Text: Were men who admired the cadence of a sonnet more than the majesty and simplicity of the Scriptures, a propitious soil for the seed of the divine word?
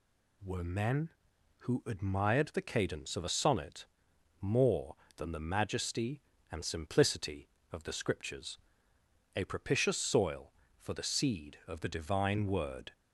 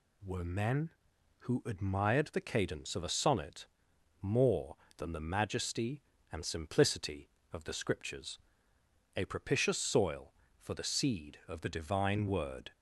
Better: neither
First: pauses between "sonnet" and "more"; noticeable; at 3.8 s; 0.54 s long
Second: pauses between "sonnet" and "more"; noticeable; at 3.6 s; 0.54 s long

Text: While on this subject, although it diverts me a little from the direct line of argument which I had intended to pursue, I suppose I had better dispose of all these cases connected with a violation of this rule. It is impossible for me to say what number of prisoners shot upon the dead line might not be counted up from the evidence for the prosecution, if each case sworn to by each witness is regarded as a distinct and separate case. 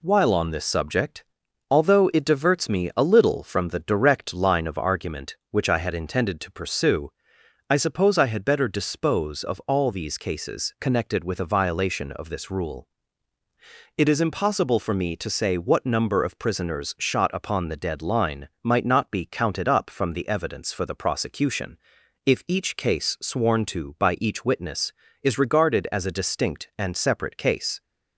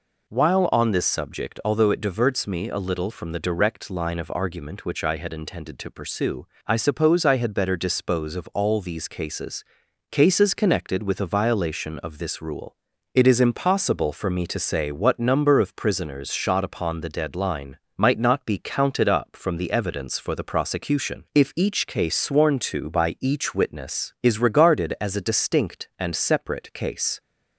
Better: first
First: none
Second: says "cases" twice; at 10.1 s // pauses between "line" and "might"; slight; at 17.7 s; 0.20 s long

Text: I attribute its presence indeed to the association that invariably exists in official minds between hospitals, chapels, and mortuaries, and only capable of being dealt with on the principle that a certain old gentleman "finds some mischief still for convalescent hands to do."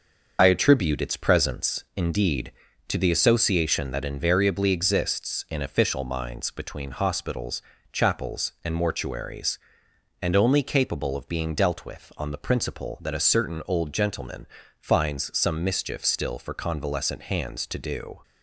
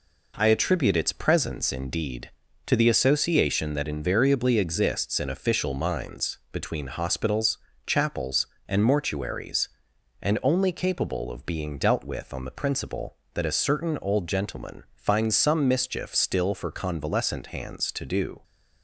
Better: second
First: loses the start of "I"; at 0.3 s; 50 ms // starts louder than the rest; until 1.4 s; 6 dB // pauses between "gentleman" and "finds"; slight; at 14.4 s; 0.32 s long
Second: none

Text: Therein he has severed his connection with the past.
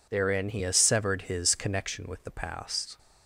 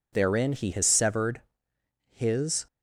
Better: first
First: none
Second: pauses between "severed" and "his"; noticeable; at 1.4 s; 0.72 s long // stops before "connection with the past"; at 2.6 s

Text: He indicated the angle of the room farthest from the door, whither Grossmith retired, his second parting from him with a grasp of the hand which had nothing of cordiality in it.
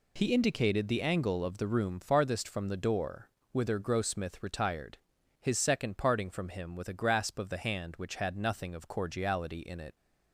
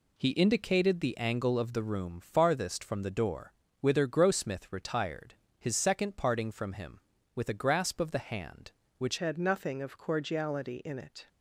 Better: first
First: none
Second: changes voice at "had"; from 9.1 s on; 2.1 s long

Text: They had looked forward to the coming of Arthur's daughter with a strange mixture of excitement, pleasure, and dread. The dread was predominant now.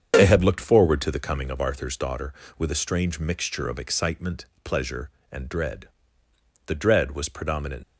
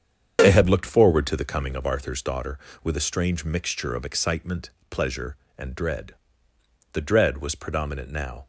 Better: second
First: starts louder than the rest; strong; until 1.1 s; 8 dB // stops before "now"; at 7.8 s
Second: starts louder than the rest; strong; until 1.4 s; 8 dB

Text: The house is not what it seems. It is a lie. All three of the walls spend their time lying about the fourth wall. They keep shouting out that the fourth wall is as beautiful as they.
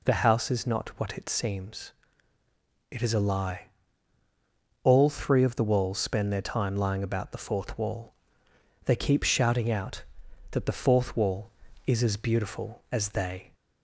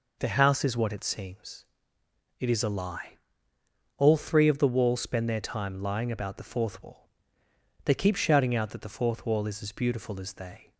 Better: first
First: none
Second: skips "not"; at 0.7 s

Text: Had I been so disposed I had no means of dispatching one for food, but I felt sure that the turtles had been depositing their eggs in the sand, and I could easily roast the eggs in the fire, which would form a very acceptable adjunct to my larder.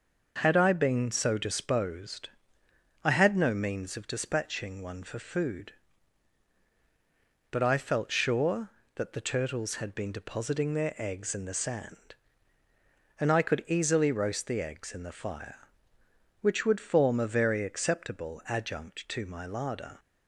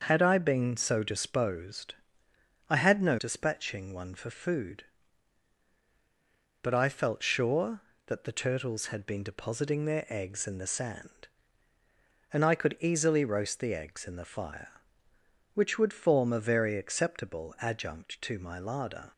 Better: first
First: pauses between "disposed" and "I"; noticeable; at 2.2 s; 0.74 s long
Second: starts louder than the rest; until 1.0 s; 6 dB // pauses between "disposed" and "I"; noticeable; at 1.9 s; 0.74 s long // skips "means of"; at 3.1 s

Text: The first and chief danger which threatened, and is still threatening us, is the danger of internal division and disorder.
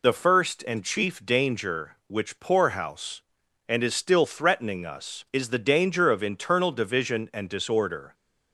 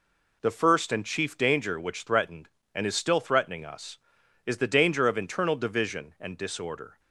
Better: second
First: says "poorhouse" for "threatened"; at 2.3 s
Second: none

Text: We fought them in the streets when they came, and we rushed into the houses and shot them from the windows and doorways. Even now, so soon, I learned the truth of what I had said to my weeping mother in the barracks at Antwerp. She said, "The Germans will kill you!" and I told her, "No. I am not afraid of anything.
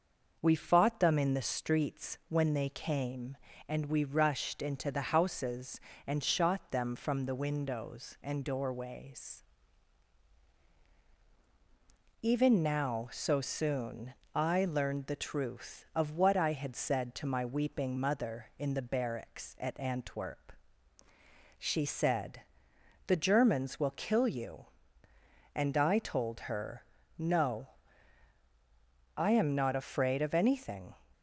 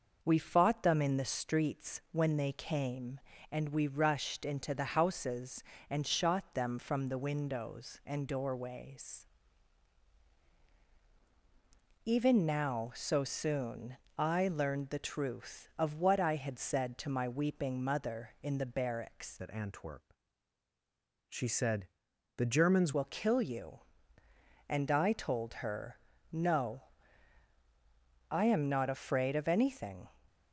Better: first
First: none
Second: changes voice from "at" to "Germans"; from 19.4 to 22.9 s; 3.5 s long

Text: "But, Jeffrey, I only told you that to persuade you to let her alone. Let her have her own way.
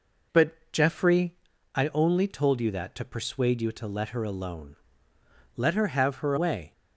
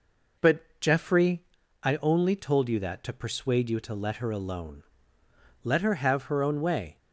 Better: second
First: skips "own"; at 6.3 s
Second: none

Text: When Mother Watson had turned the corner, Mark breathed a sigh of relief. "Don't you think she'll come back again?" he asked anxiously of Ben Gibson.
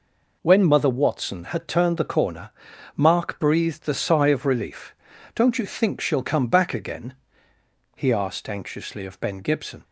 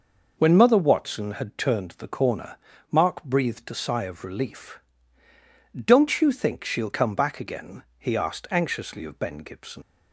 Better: first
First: none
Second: leaves "Gibson" unfinished; at 9.8 s; 65 ms

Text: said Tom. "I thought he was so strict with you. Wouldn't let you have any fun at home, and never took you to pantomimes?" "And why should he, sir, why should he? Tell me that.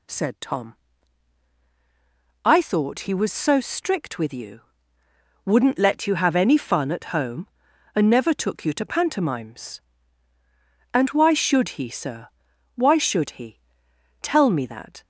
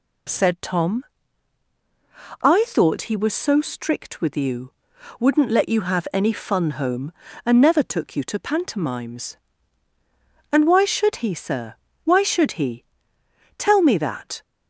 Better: first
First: none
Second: skips "at"; at 6.7 s

